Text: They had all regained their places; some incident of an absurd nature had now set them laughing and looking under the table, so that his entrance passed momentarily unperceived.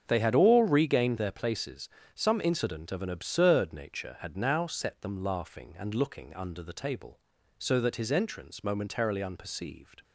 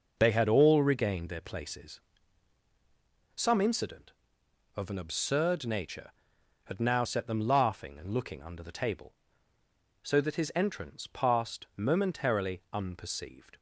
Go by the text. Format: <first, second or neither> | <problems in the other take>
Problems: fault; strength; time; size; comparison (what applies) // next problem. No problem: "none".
second | starts louder than the rest; strong; until 1.0 s; 7.5 dB // skips "passed"; at 8.6 s